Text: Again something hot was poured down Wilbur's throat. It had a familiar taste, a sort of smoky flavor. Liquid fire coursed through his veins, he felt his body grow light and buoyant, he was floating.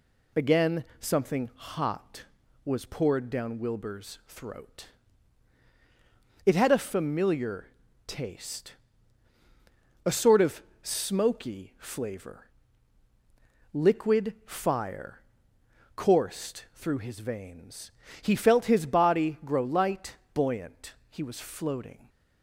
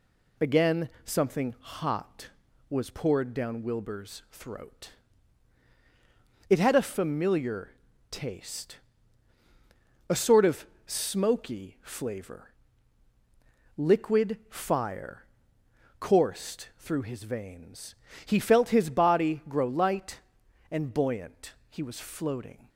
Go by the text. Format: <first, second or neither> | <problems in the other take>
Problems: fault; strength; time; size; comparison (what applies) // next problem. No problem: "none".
second | pauses between "familiar" and "taste"; at 7.6 s; 0.40 s long; also in the second // pauses between "of" and "smoky"; slight; at 10.6 s; 0.20 s long; slight in the second // pauses between "fire" and "coursed"; noticeable; at 15.2 s; 0.74 s long; noticeable in the second // skips "and"; at 20.2 s